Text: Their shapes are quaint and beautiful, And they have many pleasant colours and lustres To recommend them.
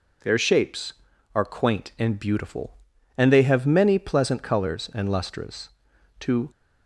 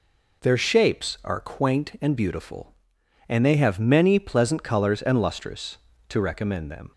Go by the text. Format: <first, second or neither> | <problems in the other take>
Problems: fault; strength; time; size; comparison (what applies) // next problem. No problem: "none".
second | stops before "recommend them"; at 6.5 s